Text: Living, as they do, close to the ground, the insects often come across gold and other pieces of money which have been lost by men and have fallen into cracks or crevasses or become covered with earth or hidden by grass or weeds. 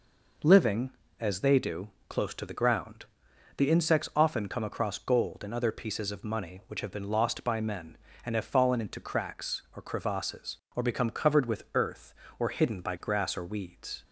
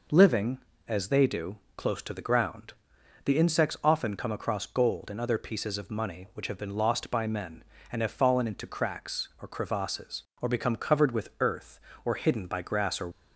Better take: first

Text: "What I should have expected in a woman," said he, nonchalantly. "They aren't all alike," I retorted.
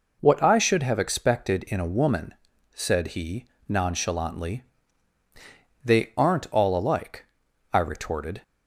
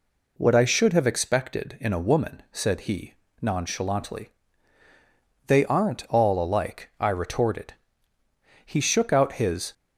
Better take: first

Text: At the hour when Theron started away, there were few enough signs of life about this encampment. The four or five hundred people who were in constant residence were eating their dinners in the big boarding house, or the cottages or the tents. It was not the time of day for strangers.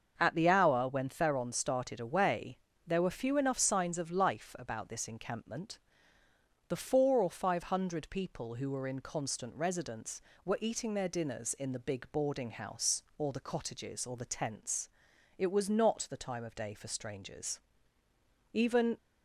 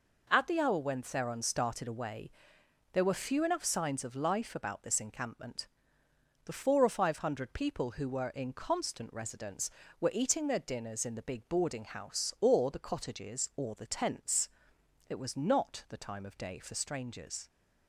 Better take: second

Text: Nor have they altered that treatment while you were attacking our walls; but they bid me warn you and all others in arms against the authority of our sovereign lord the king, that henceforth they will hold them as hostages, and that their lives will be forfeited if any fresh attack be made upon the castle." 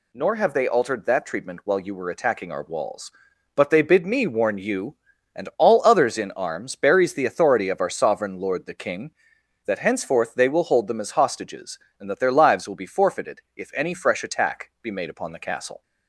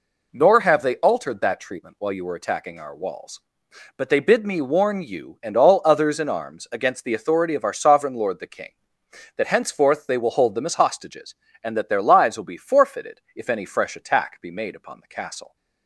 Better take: second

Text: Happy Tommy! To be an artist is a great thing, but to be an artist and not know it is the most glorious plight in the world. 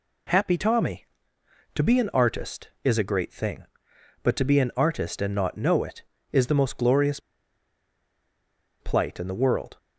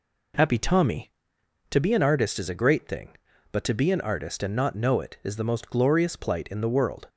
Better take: second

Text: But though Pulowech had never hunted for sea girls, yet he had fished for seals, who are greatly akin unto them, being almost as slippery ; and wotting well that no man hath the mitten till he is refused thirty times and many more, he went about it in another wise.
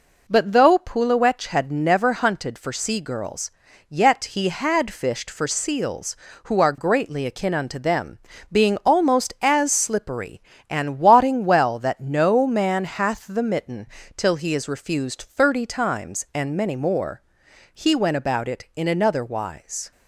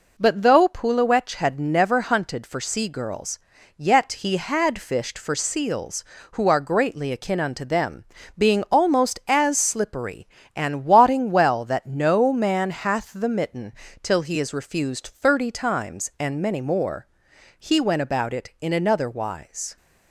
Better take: neither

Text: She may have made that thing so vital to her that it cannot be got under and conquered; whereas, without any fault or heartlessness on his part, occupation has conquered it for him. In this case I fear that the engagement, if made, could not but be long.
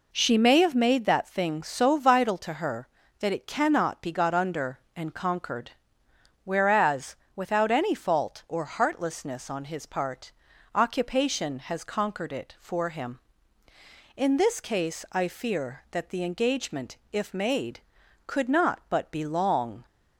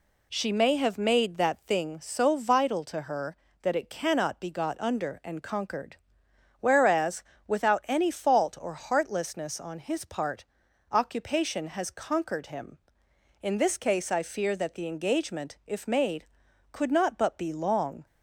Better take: first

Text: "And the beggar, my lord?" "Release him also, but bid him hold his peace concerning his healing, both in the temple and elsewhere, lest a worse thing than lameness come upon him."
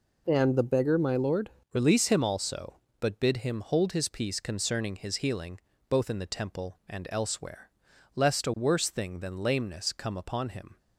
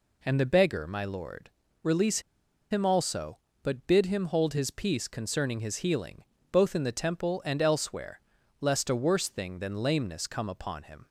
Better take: first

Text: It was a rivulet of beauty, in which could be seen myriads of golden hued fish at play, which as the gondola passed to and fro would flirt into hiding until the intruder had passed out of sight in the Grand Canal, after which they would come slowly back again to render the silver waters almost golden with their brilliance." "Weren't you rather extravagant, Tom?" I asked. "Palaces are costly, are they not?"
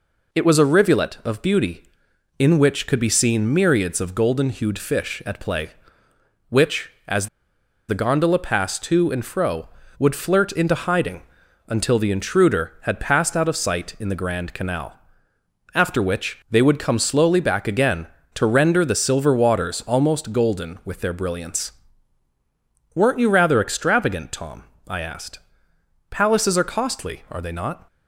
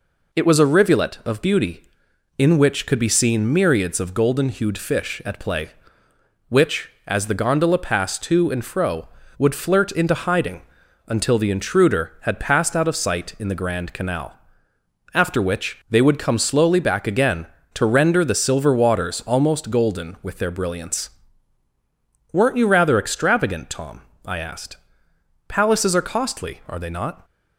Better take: second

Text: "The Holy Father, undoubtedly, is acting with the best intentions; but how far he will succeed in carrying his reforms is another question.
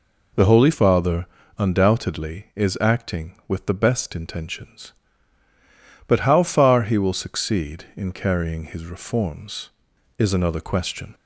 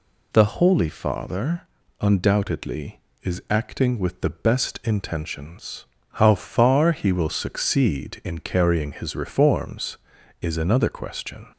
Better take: first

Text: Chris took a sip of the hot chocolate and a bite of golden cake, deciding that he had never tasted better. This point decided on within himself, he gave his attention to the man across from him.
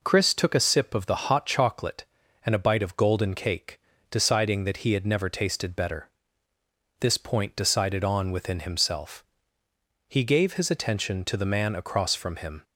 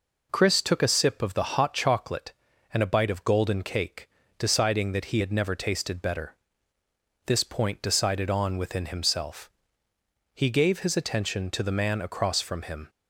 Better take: neither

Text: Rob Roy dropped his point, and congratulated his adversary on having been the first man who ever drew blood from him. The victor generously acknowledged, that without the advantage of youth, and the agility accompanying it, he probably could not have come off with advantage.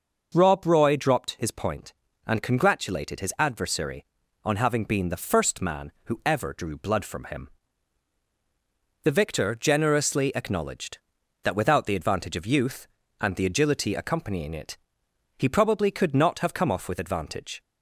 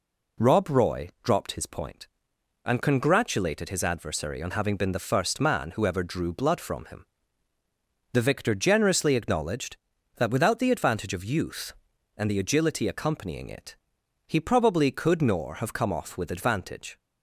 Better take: first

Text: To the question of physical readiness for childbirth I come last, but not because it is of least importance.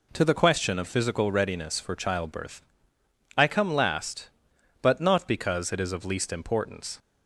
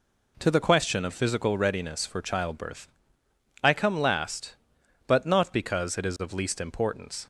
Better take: neither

